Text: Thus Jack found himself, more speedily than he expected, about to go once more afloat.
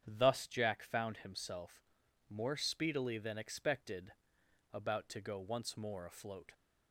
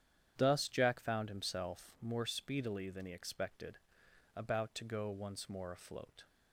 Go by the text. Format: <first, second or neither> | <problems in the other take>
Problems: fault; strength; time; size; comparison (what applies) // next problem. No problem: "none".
second | starts louder than the rest; strong; until 1.0 s; 8.5 dB; strong in the second // skips "he"; at 3.3 s